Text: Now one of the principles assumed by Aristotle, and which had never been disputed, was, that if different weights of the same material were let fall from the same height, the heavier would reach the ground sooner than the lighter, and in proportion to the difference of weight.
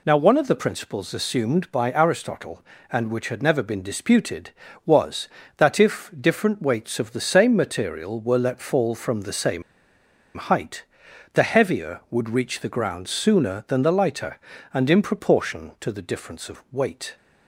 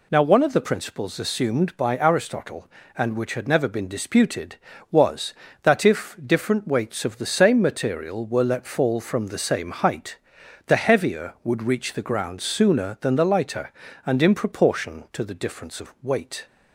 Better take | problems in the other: second | pauses between "same" and "height"; noticeable; at 9.6 s; 0.75 s long

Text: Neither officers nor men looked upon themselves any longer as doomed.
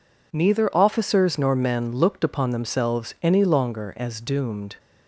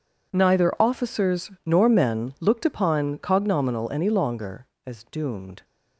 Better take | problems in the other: first | pauses between "officers" and "nor"; slight; at 1.4 s; 0.16 s long // says "cognominal" for "themselves"; at 3.1 s

